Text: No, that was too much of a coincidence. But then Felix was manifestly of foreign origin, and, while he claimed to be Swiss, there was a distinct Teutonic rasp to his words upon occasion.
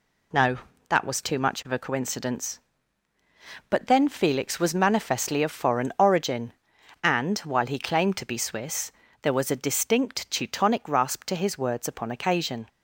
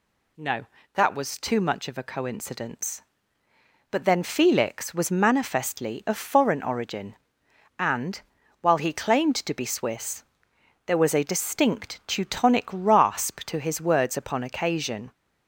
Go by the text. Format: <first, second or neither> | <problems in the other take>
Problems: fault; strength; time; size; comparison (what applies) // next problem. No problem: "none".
neither | none